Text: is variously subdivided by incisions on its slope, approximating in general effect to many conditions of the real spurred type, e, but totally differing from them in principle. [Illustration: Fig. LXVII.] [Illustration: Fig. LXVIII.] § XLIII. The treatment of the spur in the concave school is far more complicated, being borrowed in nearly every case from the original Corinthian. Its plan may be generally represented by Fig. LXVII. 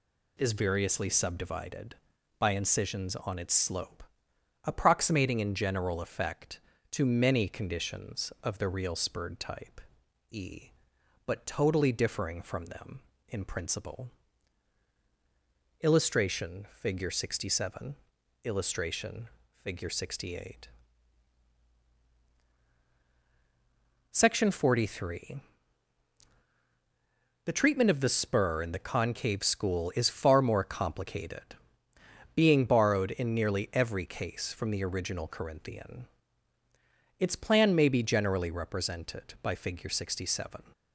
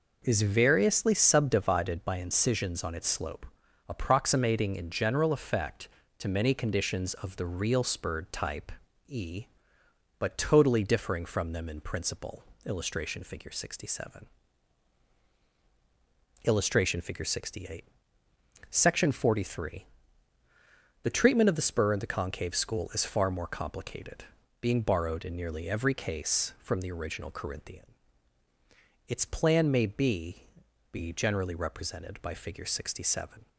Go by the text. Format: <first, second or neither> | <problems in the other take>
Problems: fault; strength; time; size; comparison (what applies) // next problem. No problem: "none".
first | says "be" twice; at 30.8 s